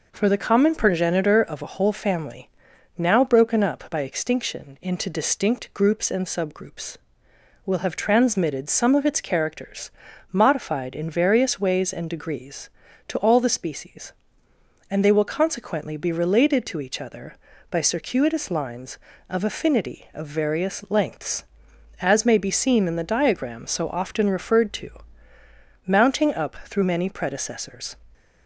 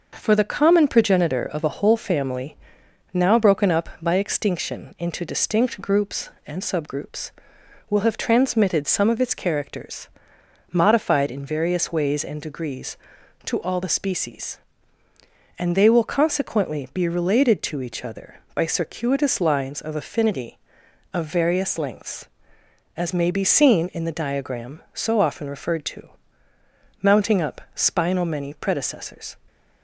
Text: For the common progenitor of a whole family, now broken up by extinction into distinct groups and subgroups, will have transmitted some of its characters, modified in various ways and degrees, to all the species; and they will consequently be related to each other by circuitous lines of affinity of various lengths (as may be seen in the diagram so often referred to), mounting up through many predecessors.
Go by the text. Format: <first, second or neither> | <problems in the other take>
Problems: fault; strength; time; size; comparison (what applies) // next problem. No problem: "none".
first | says "spinal" for "through"; at 27.7 s